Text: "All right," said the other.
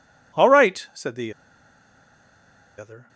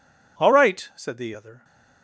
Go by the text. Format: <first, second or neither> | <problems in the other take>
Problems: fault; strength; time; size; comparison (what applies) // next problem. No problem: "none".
second | pauses between "the" and "other"; strong; at 1.3 s; 1.4 s long